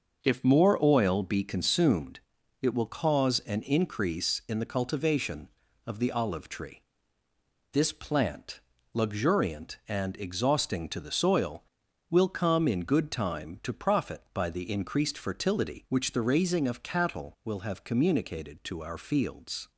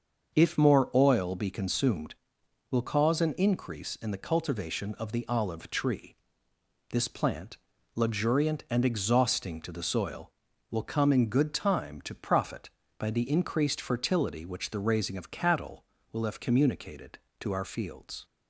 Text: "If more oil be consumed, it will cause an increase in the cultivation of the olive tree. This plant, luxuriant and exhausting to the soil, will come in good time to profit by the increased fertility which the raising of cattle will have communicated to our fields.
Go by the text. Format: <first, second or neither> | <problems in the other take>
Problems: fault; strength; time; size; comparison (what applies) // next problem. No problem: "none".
first | starts louder than the rest; until 1.4 s; 6.5 dB; also in the first // skips "it"; at 2.4 s